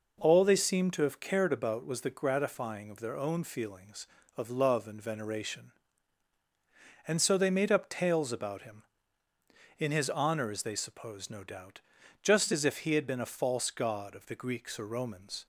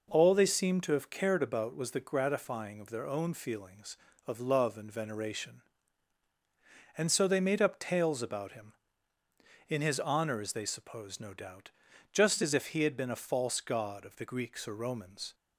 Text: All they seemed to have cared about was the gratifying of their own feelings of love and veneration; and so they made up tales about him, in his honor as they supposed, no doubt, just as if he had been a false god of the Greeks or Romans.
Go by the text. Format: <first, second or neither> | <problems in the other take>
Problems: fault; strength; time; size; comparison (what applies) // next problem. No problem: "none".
neither | none